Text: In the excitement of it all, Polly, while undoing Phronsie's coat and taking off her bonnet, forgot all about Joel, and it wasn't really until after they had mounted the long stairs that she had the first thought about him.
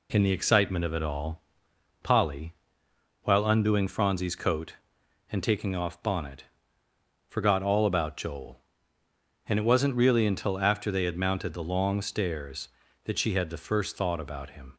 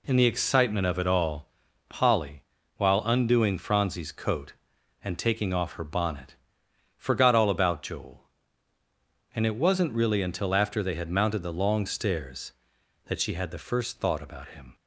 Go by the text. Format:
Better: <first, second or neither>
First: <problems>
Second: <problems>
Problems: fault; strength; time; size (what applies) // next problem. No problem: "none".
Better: second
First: skips "her"; at 6.0 s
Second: none